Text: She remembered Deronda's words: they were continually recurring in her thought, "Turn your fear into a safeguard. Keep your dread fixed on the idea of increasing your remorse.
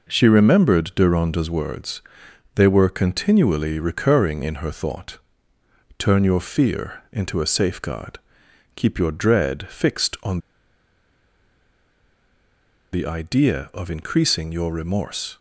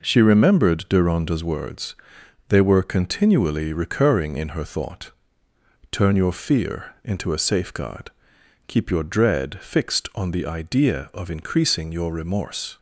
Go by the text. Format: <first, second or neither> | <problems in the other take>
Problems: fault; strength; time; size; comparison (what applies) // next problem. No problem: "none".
second | pauses between "on" and "the"; strong; at 10.3 s; 2.5 s long